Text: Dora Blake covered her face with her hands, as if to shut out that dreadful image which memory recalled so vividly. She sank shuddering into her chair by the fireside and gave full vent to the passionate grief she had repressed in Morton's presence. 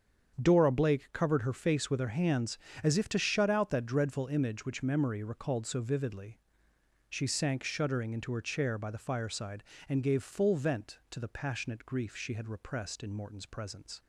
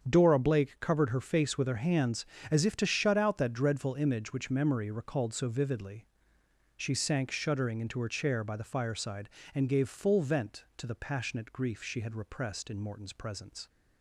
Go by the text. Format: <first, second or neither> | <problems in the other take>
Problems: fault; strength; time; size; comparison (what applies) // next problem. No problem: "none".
neither | starts louder than the rest; strong; the same in both